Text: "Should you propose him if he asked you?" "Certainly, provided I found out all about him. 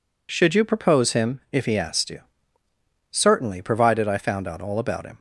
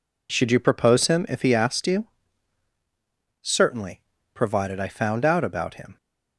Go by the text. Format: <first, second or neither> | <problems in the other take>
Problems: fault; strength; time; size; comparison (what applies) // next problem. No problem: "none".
first | skips "all"; at 5.4 s